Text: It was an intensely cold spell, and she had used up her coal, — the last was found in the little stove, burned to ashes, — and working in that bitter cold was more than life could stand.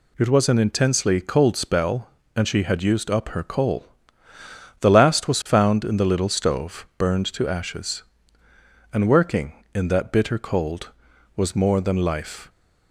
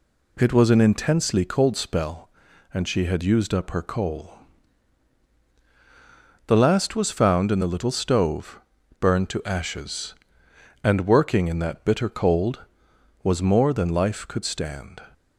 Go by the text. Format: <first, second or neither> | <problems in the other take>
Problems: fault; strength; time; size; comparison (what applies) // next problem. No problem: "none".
second | stops before "could stand"; at 12.4 s